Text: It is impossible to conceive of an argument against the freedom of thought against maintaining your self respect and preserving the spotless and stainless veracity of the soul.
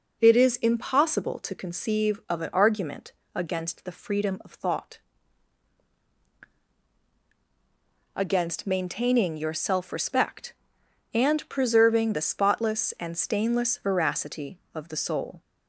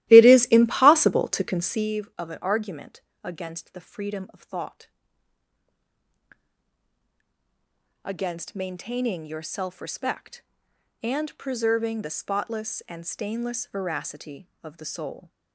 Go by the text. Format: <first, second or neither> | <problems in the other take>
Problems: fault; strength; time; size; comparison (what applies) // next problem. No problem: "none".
first | starts louder than the rest; strong; until 1.9 s; 15.5 dB // pauses between "argument" and "against"; slight; at 3.0 s; 0.22 s long; slight in the first // pauses between "thought" and "against"; strong; at 4.8 s; 3.1 s long; strong in the first